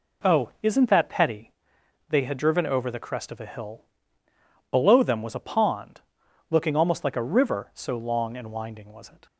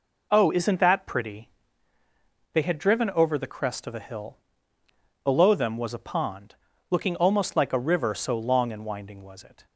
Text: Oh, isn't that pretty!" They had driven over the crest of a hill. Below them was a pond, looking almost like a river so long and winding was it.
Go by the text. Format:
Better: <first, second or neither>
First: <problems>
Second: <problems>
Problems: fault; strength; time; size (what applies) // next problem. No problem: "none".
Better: second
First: says "petty" for "pretty"; at 1.0 s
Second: none